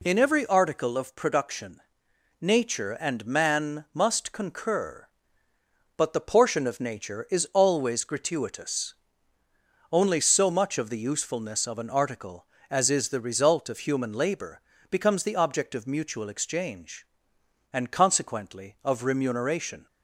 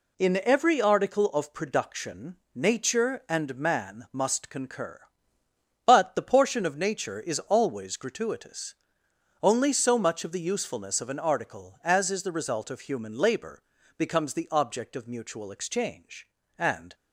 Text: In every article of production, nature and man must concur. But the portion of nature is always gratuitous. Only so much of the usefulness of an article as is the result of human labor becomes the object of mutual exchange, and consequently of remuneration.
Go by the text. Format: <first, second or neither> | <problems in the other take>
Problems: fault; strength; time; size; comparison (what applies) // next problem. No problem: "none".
first | pauses between "labor" and "becomes"; slight; at 13.6 s; 0.36 s long; slight in the first // stops before "consequently of remuneration"; at 16.9 s